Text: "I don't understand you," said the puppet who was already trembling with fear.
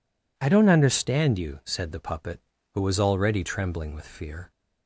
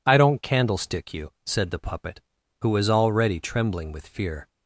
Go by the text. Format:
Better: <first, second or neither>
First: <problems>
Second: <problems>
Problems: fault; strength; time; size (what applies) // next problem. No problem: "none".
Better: first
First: none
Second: says "candlestick" for "understand"; at 0.4 s